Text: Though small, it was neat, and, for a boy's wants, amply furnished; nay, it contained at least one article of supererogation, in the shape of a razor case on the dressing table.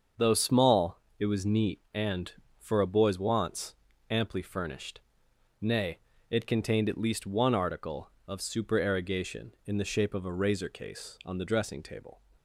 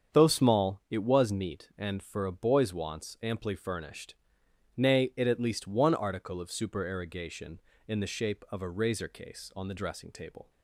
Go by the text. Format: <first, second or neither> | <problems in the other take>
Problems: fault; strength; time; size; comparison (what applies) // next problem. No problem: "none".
first | starts louder than the rest; strong; until 1.2 s; 7.5 dB; also in the first // skips "contained"; at 5.2 s